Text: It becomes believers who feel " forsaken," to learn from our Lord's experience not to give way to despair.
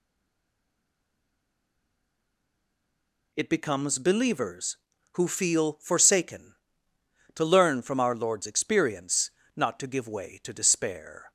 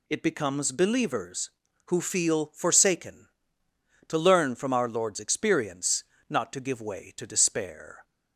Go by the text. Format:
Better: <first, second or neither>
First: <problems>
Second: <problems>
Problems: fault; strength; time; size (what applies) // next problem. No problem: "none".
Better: second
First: stays silent before the first word; strong; until 3.3 s; 3.3 s long // pauses between "experience" and "not"; slight; at 9.3 s; 0.26 s long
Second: pauses between "experience" and "not"; slight; at 6.0 s; 0.26 s long